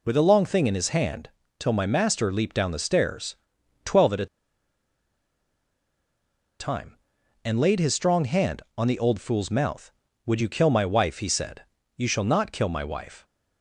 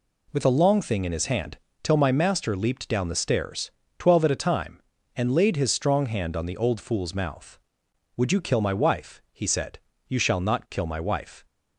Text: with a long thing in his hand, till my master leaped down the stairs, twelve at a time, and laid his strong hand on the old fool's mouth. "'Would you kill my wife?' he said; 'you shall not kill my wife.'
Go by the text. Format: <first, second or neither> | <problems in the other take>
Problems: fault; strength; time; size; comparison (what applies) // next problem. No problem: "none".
second | pauses between "a" and "time"; strong; at 4.2 s; 2.3 s long